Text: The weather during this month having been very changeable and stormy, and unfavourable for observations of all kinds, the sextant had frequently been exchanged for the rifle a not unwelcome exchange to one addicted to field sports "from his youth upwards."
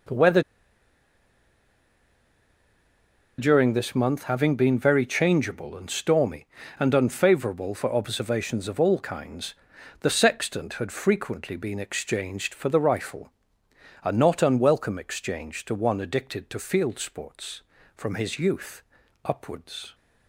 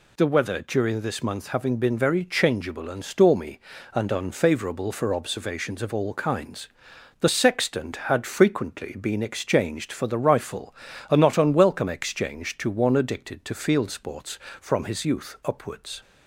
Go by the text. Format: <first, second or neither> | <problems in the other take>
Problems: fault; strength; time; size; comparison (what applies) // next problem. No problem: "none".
second | pauses between "weather" and "during"; strong; at 0.4 s; 2.9 s long // pauses between "rifle" and "a"; noticeable; at 13.2 s; 0.76 s long; slight in the second // pauses between "youth" and "upwards"; at 18.8 s; 0.42 s long